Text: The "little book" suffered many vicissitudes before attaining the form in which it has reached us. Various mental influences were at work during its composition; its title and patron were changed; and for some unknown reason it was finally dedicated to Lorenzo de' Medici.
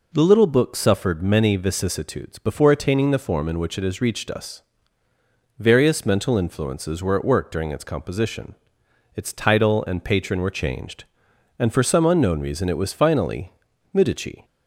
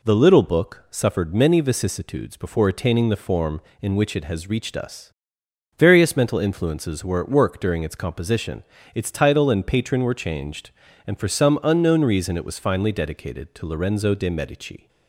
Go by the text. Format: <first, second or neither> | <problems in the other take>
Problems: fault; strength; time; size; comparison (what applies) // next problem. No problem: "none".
second | skips "dedicated to Lorenzo de"; at 13.7 s